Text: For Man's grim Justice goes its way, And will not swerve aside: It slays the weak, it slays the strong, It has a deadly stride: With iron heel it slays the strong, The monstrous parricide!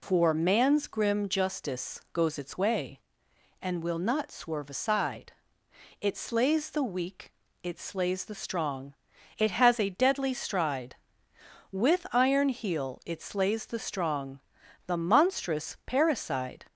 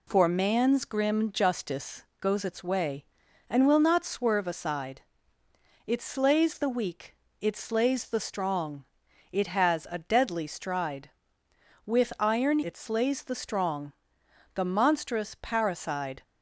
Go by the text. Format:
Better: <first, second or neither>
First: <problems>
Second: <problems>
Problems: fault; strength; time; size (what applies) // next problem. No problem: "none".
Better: first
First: none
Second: pauses between "Justice" and "goes"; slight; at 2.0 s; 0.16 s long // skips "heel"; at 12.6 s